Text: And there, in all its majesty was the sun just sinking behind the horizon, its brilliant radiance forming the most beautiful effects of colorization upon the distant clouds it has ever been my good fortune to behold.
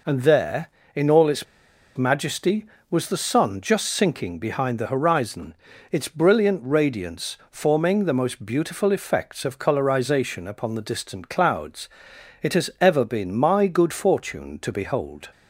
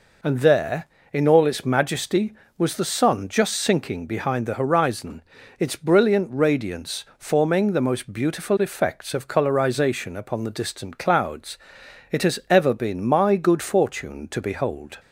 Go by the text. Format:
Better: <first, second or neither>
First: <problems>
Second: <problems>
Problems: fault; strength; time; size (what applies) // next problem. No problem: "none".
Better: second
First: pauses between "its" and "majesty"; noticeable; at 1.4 s; 0.52 s long // pauses between "clouds" and "it"; noticeable; at 11.8 s; 0.54 s long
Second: pauses between "clouds" and "it"; noticeable; at 11.5 s; 0.54 s long